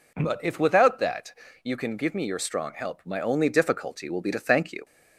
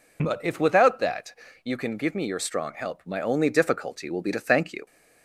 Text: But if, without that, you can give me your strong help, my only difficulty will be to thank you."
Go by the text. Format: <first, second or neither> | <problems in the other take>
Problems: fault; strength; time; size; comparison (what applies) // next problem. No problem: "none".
first | loses the start of "But"; at 0.1 s; 45 ms